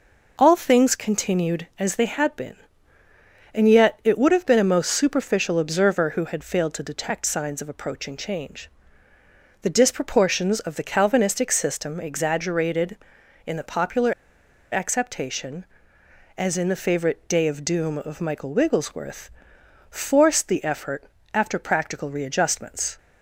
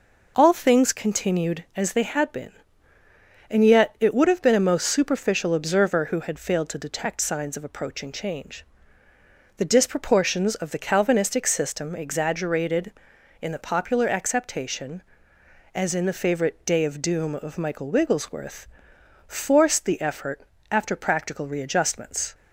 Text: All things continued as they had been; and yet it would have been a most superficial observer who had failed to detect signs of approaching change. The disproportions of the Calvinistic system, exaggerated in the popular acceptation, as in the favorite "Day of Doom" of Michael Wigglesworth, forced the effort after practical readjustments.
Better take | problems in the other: second | pauses between "popular" and "acceptation"; noticeable; at 14.1 s; 0.60 s long // pauses between "effort" and "after"; slight; at 21.0 s; 0.28 s long; slight in the second

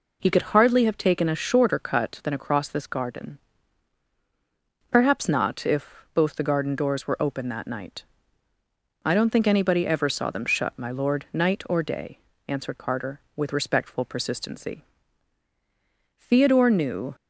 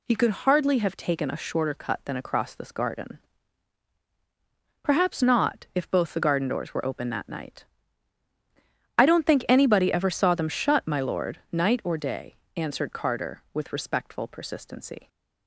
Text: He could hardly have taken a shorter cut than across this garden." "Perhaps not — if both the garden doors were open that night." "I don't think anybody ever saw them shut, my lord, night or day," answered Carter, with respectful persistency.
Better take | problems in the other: second | goes on to say "Theodore knew"; noticeable; from 16.1 s on; 0.96 s long

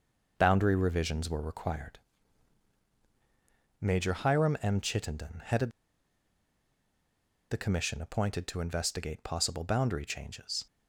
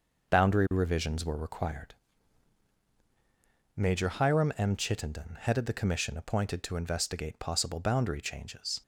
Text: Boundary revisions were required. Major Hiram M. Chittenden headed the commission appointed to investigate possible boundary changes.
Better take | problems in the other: second | pauses between "headed" and "the"; strong; at 5.7 s; 1.8 s long

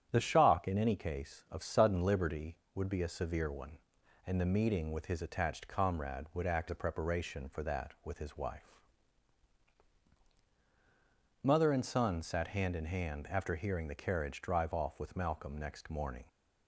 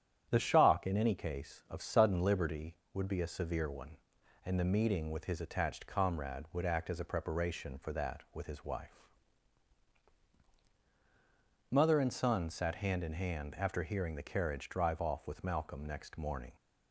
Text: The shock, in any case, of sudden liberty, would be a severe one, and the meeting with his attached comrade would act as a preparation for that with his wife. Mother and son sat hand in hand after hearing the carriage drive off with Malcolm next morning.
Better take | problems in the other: second | starts louder than the rest; strong; until 1.1 s; 7.5 dB; strong in the second // skips "as"; at 6.6 s

